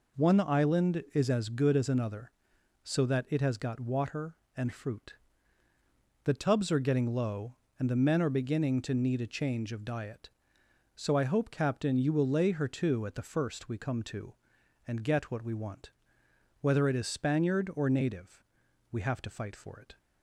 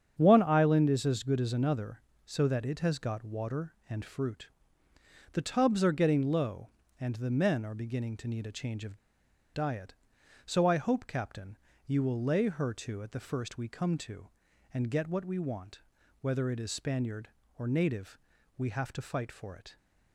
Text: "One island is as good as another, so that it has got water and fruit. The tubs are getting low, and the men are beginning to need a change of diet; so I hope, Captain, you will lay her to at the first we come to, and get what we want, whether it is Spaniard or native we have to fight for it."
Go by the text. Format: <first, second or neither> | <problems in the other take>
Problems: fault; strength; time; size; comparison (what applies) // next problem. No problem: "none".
first | starts louder than the rest; strong; until 1.1 s; 8 dB // pauses between "of" and "diet"; noticeable; at 8.9 s; 0.56 s long // pauses between "native" and "we"; at 18.1 s; 0.40 s long; noticeable in the first